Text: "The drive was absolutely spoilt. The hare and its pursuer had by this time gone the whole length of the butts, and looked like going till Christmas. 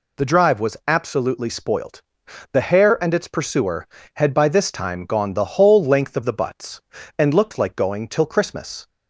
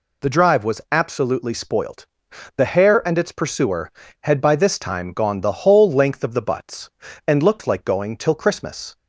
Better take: neither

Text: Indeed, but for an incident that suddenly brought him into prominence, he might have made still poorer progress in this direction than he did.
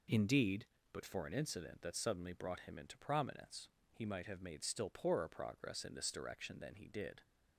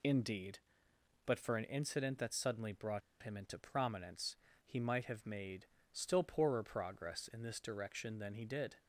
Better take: first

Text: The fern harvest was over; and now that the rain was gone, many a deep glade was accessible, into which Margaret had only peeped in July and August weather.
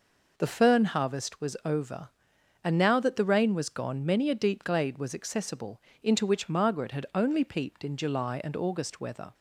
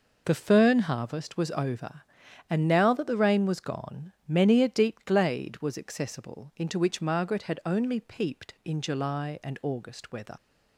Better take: first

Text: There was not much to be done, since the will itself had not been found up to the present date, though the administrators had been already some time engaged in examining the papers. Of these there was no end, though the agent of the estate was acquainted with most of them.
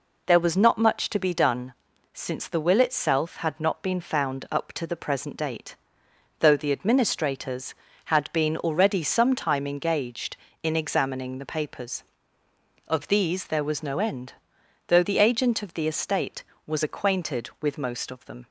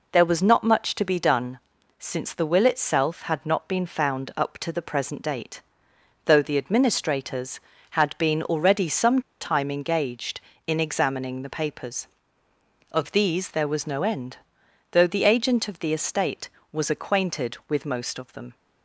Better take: first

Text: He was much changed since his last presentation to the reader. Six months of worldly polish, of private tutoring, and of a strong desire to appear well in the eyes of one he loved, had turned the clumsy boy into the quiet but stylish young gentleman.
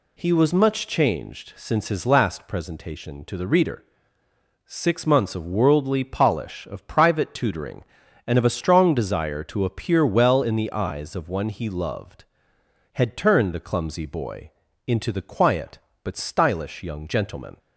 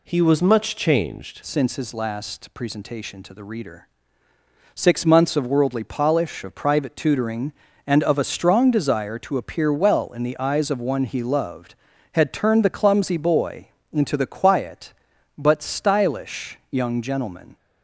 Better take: first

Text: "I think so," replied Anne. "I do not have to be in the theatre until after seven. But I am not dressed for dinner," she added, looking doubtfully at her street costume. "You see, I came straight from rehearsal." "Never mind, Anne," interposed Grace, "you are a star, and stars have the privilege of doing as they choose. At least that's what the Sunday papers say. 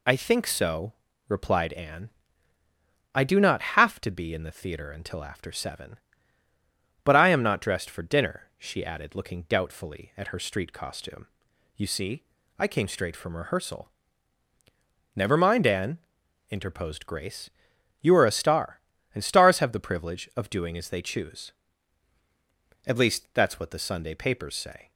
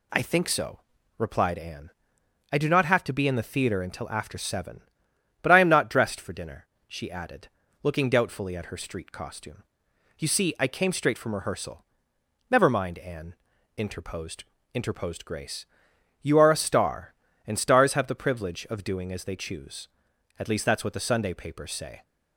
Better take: first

